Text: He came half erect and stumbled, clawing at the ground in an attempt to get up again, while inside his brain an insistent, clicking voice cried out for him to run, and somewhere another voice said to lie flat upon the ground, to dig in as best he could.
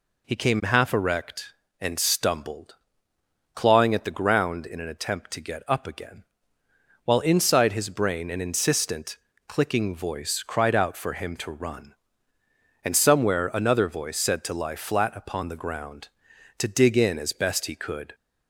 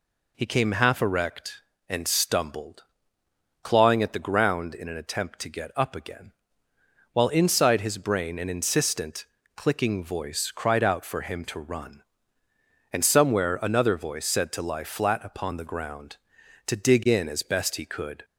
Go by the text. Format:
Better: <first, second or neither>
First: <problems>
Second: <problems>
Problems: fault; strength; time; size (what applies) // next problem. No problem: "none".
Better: neither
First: none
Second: none